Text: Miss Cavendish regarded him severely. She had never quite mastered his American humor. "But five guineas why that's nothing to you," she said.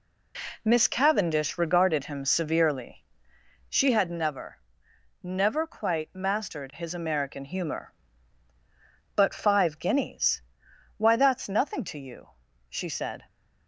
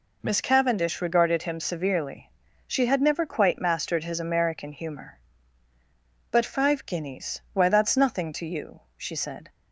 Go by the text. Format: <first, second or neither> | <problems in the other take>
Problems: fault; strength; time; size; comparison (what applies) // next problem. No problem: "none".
second | says "never" twice; at 5.2 s // pauses between "guineas" and "why"; noticeable; at 10.4 s; 0.54 s long